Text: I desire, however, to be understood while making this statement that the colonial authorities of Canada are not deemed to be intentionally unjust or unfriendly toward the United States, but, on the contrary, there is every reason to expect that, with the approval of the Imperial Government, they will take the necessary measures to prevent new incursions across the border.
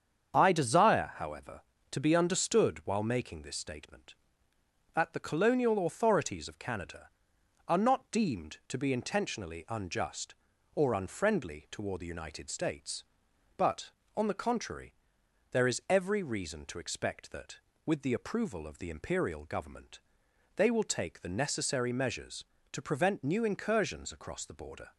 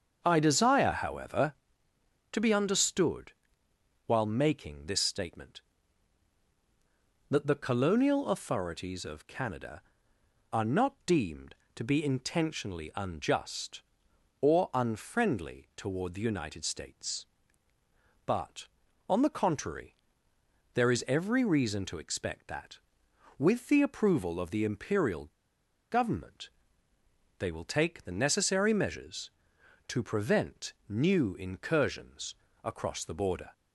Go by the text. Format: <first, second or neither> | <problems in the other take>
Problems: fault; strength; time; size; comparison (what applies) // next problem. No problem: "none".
first | starts louder than the rest; until 1.2 s; 6.5 dB; strong in the first // pauses between "understood" and "while"; noticeable; at 3.3 s; 0.74 s long // pauses between "Imperial" and "Government"; noticeable; at 25.2 s; 0.61 s long // pauses between "prevent" and "new"; slight; at 30.7 s; 0.16 s long // pauses between "incursions" and "across"; slight; at 32.3 s; 0.30 s long